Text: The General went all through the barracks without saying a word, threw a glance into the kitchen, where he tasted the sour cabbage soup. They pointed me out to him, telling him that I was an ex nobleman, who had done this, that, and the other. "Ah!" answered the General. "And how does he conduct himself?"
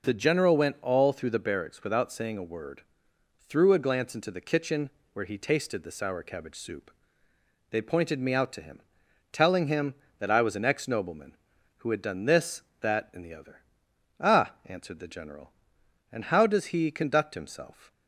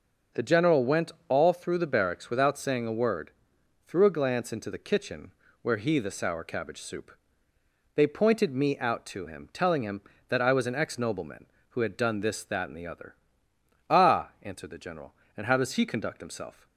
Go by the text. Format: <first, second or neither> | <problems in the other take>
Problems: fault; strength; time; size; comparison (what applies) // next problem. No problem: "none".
first | pauses between "went" and "all"; slight; at 1.1 s; 0.18 s long // skips "tasted"; at 5.9 s